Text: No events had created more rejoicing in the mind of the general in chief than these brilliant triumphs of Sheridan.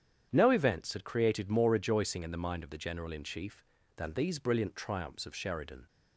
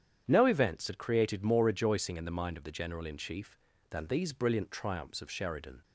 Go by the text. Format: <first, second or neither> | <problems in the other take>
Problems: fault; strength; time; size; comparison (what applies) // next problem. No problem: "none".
neither | starts louder than the rest; strong; the same in both